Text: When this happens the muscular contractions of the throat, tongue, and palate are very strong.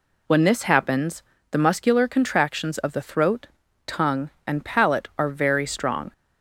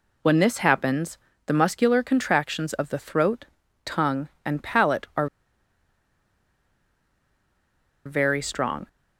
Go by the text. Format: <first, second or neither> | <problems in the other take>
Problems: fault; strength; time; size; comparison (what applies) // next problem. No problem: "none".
first | pauses between "happens" and "the"; slight; at 1.1 s; 0.30 s long; slight in the first // pauses between "are" and "very"; strong; at 5.2 s; 2.7 s long